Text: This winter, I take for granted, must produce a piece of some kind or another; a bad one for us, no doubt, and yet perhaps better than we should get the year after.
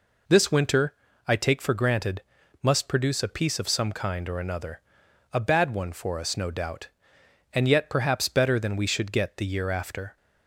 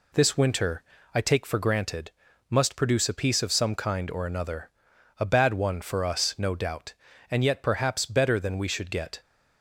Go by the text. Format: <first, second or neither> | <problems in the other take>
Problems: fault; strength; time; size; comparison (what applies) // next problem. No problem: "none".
first | stops before "the year after"; at 9.2 s